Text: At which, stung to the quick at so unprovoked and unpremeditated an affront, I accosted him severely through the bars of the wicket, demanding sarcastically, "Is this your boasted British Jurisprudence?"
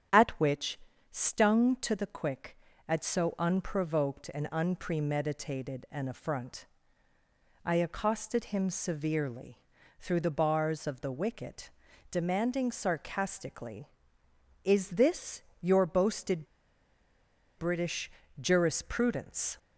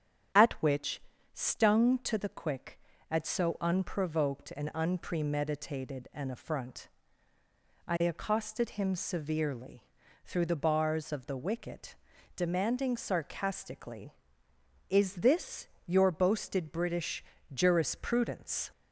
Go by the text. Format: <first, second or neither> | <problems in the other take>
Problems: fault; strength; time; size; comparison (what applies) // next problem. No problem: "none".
second | starts louder than the rest; strong; until 1.5 s; 8.5 dB; strong in the second // pauses between "severely" and "through"; at 9.5 s; 0.42 s long; also in the second // pauses between "this" and "your"; slight; at 15.4 s; 0.18 s long; slight in the second // pauses between "boasted" and "British"; at 16.4 s; 1.1 s long // pauses between "British" and "Jurisprudence"; slight; at 18.1 s; 0.30 s long; slight in the second